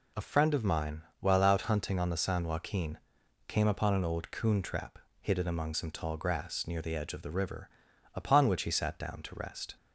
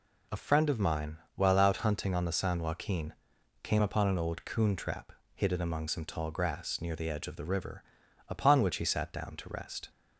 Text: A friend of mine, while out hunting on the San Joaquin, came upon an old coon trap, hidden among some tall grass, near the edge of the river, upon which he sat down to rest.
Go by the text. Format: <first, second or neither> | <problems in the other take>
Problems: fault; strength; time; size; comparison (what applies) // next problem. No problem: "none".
neither | none